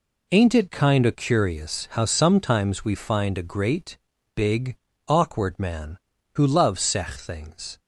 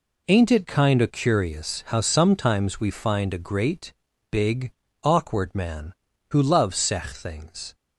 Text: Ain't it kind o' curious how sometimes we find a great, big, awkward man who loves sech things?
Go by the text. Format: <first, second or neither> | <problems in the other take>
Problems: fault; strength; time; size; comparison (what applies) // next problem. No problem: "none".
neither | none